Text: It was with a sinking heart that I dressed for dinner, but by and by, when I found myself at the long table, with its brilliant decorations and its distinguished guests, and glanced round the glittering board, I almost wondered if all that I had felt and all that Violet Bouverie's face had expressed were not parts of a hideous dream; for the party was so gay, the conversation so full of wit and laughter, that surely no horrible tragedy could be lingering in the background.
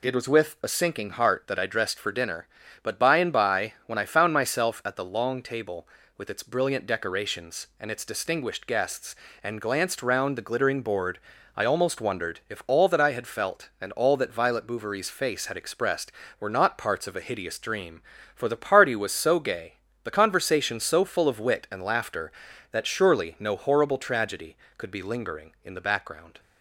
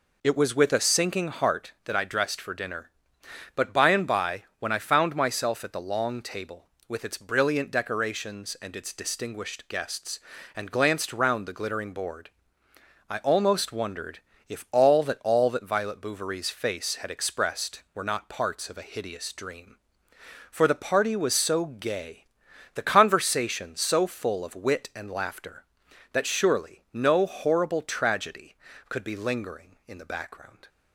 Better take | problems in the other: first | pauses between "wondered" and "if"; slight; at 14.1 s; 0.30 s long // skips "I had felt and"; at 15.1 s

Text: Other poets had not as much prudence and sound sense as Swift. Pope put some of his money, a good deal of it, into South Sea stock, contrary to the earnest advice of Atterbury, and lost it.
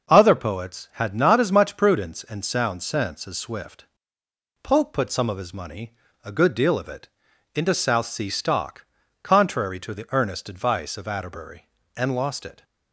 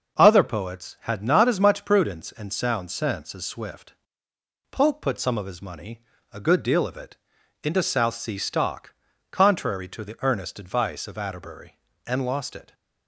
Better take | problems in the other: neither | none

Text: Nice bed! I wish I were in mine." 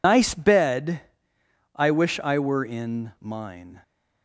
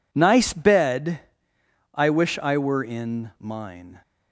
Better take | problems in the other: second | loses the start of "Nice"; at 0.0 s; 100 ms

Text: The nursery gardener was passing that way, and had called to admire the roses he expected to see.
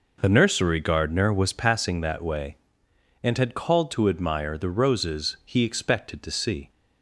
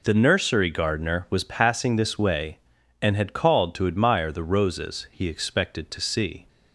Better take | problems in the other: first | says "this" for "that"; at 1.9 s

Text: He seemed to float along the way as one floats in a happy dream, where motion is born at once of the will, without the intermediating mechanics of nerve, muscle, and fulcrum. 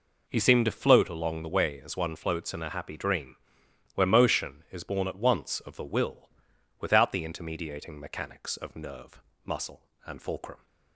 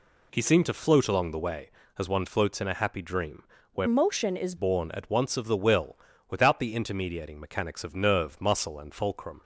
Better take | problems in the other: first | changes voice from "motion" to "is"; from 3.8 to 4.5 s; 0.7 s long

